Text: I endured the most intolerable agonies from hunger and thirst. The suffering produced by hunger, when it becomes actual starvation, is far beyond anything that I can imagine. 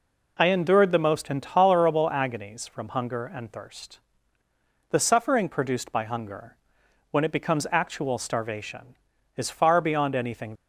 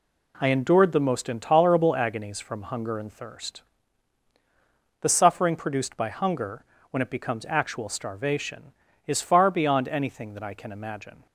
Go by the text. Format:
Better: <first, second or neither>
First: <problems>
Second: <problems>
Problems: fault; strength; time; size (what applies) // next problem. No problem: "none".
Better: second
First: stops before "that I can imagine"; at 10.5 s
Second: none